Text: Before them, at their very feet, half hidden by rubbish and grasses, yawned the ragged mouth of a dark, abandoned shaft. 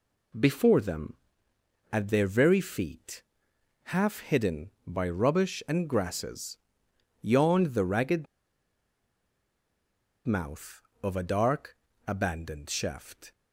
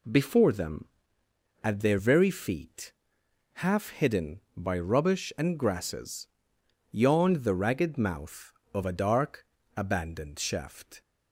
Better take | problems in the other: second | pauses between "ragged" and "mouth"; strong; at 8.2 s; 2.0 s long

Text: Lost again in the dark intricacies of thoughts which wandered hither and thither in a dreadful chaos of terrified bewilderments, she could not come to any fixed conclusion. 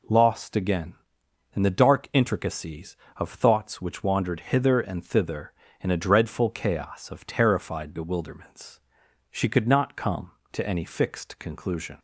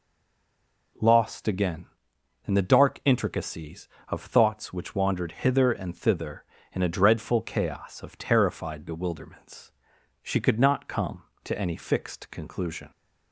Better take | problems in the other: first | stays silent before the first word; slight; until 0.9 s; 0.9 s long

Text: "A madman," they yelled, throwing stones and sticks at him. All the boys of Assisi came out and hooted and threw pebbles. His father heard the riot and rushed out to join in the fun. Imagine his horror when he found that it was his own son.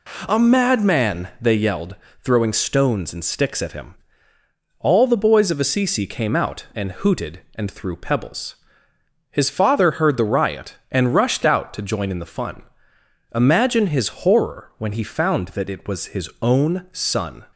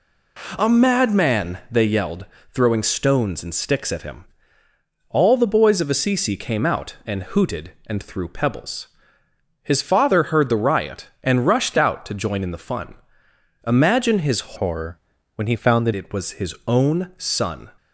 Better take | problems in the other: first | changes voice from "horror" to "that"; from 14.5 to 15.9 s; 1.4 s long // pauses between "horror" and "when"; at 14.9 s; 0.38 s long

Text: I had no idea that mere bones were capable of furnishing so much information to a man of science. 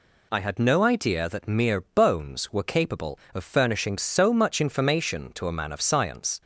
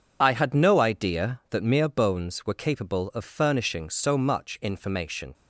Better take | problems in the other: first | stops before "to a man of science"; at 5.3 s

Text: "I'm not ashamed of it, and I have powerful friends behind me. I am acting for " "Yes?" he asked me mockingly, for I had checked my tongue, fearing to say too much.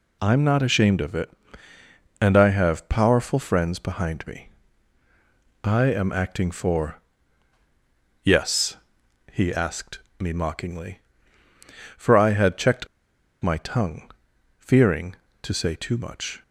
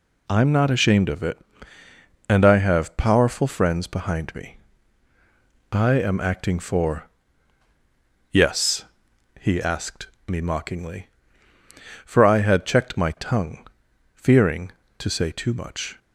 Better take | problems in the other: second | pauses between "asked" and "me"; slight; at 10.0 s; 0.18 s long; slight in the second // pauses between "checked" and "my"; noticeable; at 12.8 s; 0.54 s long

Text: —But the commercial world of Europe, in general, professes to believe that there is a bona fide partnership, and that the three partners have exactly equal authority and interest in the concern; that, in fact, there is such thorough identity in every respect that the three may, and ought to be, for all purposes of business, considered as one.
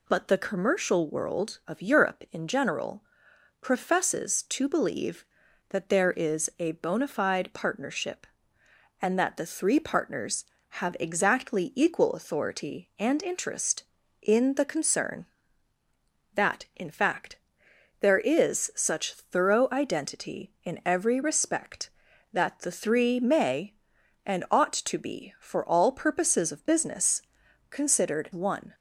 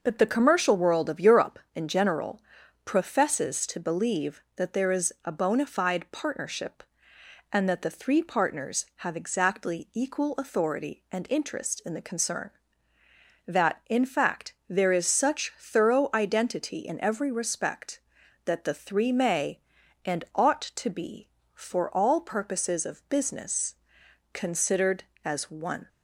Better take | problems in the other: second | skips "as"; at 28.3 s

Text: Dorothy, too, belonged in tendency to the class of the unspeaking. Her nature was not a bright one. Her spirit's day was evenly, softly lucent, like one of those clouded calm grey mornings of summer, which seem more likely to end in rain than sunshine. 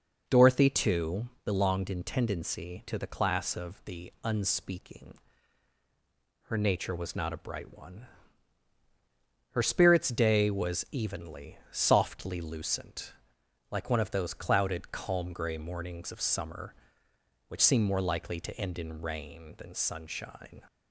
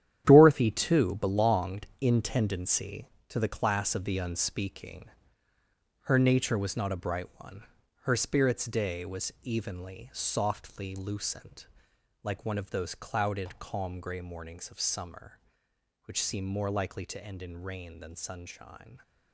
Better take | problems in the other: first | gets quieter; strong; throughout; 11 dB

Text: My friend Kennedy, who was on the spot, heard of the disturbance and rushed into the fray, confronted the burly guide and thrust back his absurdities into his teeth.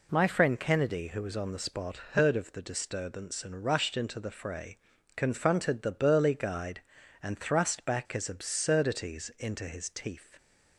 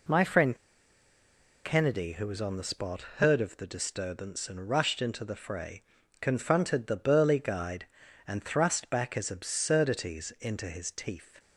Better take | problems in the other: first | pauses between "friend" and "Kennedy"; at 0.5 s; 1.0 s long

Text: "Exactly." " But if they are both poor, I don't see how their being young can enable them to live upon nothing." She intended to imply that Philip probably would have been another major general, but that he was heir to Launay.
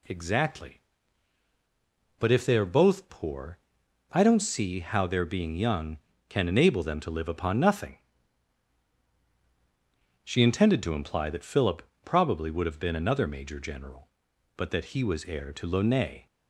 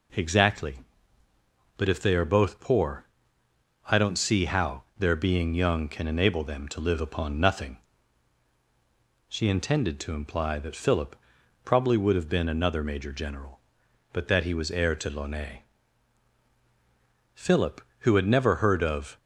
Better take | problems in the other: first | pauses between "how" and "their"; slight; at 4.8 s; 0.16 s long // pauses between "Philip" and "probably"; noticeable; at 11.1 s; 0.48 s long; slight in the first // goes on to say "Philip who had never heard of"; strong; from 17.3 s on; 1.8 s long

